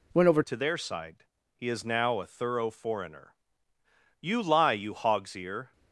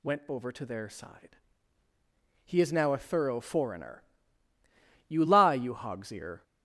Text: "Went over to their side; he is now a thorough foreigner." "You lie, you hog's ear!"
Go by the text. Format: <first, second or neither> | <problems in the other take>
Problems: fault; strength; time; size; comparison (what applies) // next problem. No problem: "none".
second | changes voice at "to"; from 0.4 s on; 5.3 s long